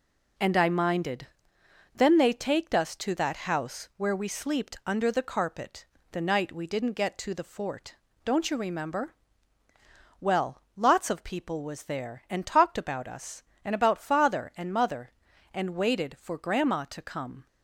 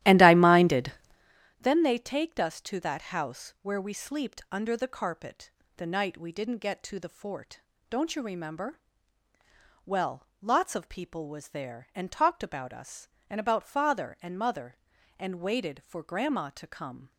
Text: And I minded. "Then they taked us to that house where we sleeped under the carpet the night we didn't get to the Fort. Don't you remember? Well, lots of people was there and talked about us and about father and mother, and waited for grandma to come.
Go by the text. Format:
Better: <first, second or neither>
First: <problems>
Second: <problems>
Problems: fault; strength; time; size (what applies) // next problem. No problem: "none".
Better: first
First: pauses between "carpet" and "the"; slight; at 5.8 s; 0.26 s long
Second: starts louder than the rest; strong; until 1.4 s; 13 dB // pauses between "carpet" and "the"; slight; at 5.5 s; 0.26 s long